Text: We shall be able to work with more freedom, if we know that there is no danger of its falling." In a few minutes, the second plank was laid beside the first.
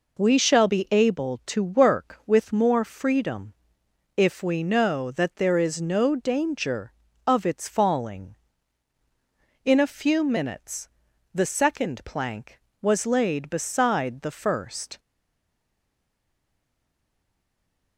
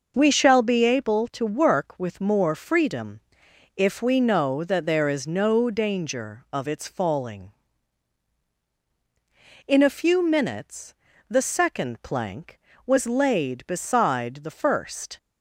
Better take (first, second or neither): second